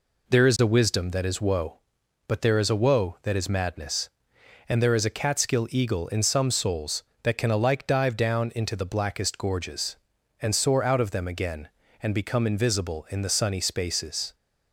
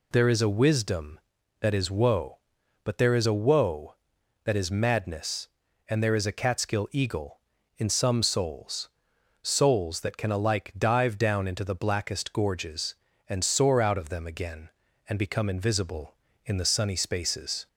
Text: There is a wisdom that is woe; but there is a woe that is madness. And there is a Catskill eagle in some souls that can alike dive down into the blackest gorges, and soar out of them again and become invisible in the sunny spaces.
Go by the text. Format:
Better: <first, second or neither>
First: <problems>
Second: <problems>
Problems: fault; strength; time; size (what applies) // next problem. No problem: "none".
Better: first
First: none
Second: says "souls" twice; at 9.4 s